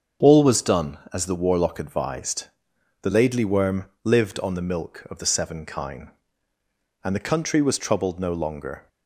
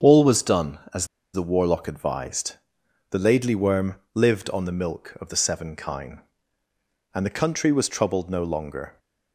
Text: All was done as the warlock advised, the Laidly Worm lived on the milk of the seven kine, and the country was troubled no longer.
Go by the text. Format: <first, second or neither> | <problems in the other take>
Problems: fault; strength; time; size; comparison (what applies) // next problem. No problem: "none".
first | starts louder than the rest; until 1.4 s; 7 dB; also in the first // pauses between "as" and "the"; slight; at 1.0 s; 0.27 s long // pauses between "Worm" and "lived"; slight; at 3.9 s; 0.18 s long; slight in the first